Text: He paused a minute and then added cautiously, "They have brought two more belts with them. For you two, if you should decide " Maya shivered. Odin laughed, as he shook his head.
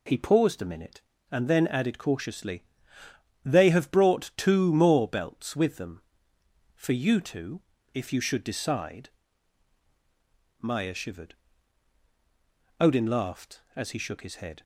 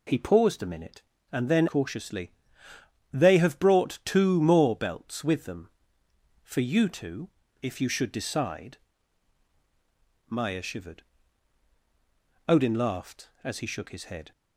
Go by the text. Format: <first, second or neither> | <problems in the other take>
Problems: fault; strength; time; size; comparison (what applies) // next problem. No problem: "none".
first | skips "added"; at 1.6 s